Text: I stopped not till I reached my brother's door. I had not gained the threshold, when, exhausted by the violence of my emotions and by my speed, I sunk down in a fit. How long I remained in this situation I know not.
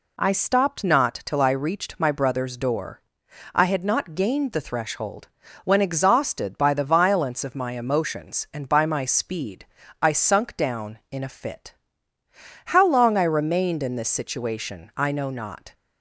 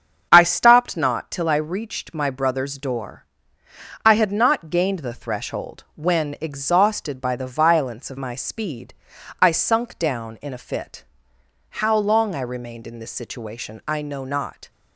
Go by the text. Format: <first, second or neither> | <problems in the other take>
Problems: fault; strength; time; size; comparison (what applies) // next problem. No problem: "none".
first | starts louder than the rest; strong; until 1.3 s; 7.5 dB // skips "my emotions and by"; at 8.1 s